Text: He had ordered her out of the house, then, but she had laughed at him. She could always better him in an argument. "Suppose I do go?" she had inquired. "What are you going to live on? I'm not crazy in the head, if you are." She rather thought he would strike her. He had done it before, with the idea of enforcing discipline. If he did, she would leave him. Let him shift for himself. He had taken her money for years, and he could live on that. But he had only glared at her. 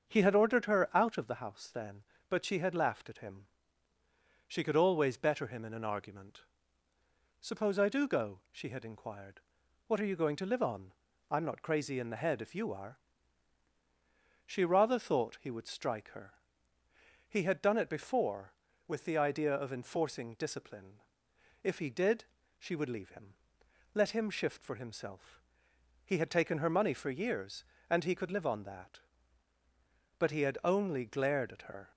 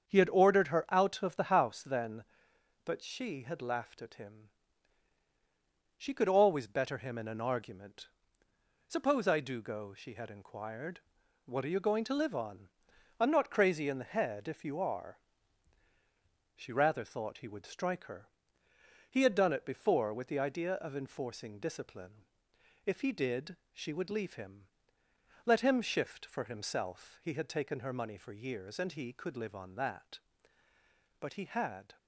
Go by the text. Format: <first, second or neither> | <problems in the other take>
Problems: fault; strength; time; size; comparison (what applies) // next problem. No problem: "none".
first | starts louder than the rest; strong; until 1.1 s; 7.5 dB; also in the first // stops before "only glared at her"; at 31.9 s